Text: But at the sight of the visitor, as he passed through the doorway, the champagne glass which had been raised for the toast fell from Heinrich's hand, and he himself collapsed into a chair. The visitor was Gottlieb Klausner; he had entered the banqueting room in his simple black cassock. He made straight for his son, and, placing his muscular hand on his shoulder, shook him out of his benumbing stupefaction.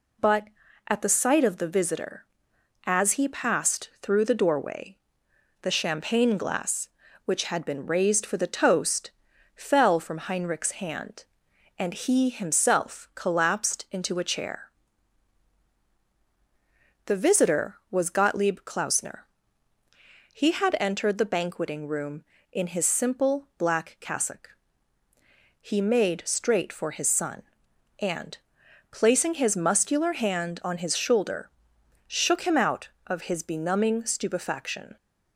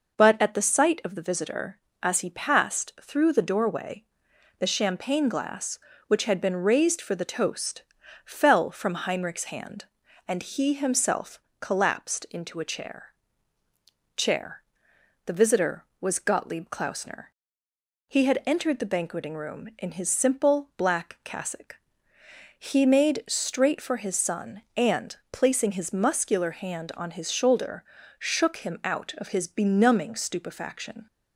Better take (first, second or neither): first